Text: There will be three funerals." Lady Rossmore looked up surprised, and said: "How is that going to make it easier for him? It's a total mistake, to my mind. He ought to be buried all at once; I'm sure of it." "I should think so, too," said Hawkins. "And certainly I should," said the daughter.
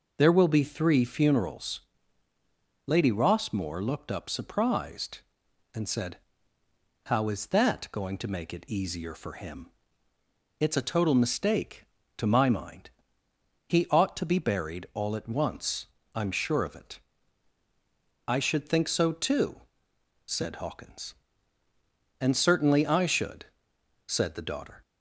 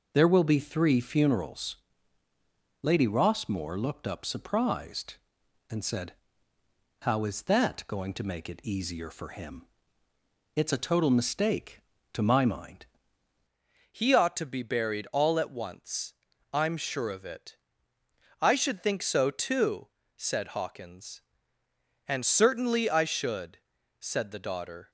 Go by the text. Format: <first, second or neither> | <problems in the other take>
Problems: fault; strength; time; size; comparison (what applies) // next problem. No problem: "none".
first | changes voice at "He"; from 13.8 s on; 11.0 s long